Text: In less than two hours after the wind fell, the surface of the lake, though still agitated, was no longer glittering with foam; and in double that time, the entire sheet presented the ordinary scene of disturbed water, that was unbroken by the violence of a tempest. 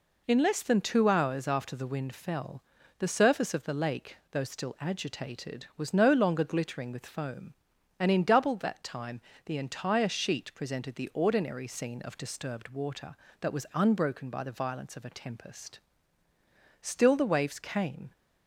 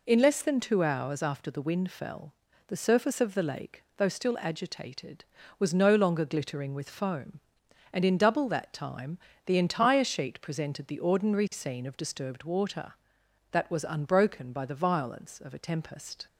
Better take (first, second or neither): second